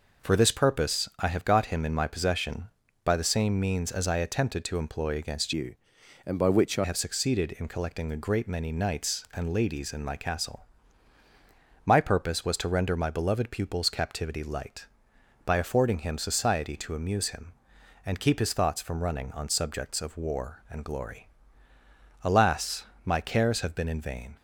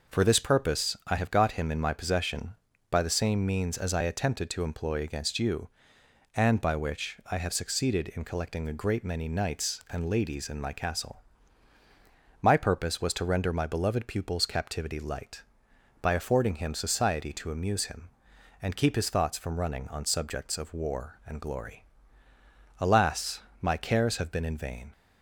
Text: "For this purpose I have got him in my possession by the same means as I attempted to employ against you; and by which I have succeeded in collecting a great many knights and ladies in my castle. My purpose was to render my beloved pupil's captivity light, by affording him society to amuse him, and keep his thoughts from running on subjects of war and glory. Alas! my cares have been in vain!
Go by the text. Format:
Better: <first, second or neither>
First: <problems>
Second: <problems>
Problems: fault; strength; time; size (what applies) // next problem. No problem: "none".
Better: second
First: changes voice from "you" to "I"; from 5.5 to 6.8 s; 1.3 s long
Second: none